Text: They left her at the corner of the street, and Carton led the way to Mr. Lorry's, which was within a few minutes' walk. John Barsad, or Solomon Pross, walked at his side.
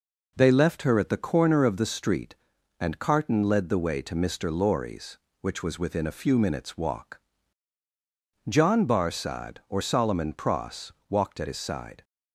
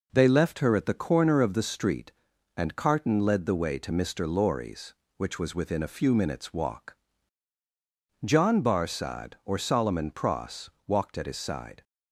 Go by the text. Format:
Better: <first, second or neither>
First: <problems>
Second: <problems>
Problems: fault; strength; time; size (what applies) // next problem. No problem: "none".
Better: neither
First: none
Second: none